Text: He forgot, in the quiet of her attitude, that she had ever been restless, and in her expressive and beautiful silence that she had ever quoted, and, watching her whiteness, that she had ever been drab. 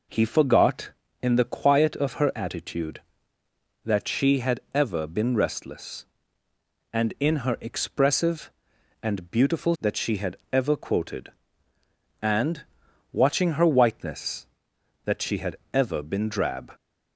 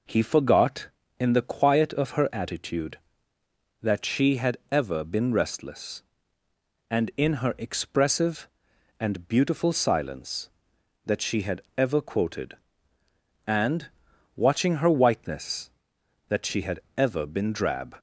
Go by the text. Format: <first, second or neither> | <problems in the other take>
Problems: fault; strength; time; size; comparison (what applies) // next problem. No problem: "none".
second | skips "silence"; at 9.7 s // pauses between "had" and "ever"; slight; at 10.3 s; 0.16 s long; slight in the second // pauses between "had" and "ever"; slight; at 15.5 s; 0.16 s long; slight in the second